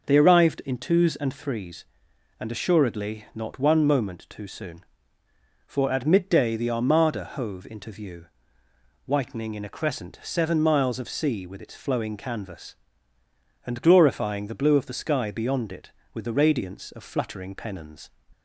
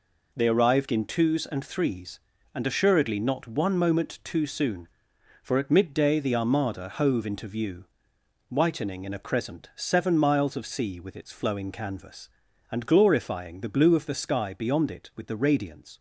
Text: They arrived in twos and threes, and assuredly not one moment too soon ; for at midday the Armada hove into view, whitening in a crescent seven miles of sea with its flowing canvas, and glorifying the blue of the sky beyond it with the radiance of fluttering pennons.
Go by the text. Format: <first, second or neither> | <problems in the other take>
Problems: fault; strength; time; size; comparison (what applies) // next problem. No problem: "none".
first | stops before "of fluttering pennons"; at 15.9 s